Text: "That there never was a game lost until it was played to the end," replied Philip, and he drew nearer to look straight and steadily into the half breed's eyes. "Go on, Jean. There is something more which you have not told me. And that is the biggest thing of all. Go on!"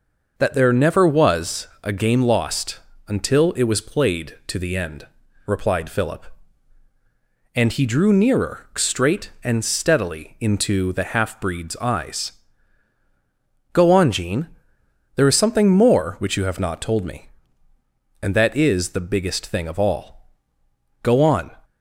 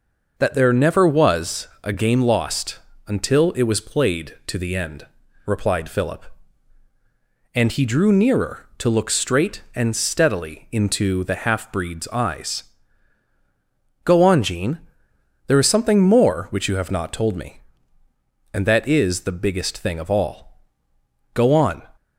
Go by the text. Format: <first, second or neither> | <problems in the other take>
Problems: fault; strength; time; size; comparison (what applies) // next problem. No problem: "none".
second | pauses between "was" and "a"; slight; at 1.6 s; 0.16 s long; slight in the second // pauses between "lost" and "until"; slight; at 2.8 s; 0.28 s long; slight in the second // skips "to look"; at 8.7 s